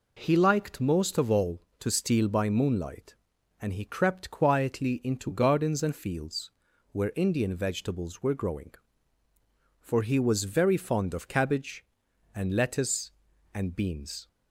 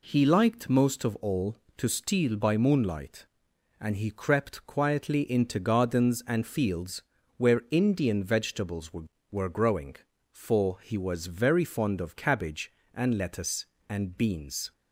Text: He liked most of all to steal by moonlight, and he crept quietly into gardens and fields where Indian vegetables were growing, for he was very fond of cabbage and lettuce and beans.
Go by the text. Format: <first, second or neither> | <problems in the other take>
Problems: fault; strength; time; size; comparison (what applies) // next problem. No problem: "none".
first | pauses between "fields" and "where"; slight; at 7.0 s; 0.36 s long; also in the first // says "were" twice; at 9.3 s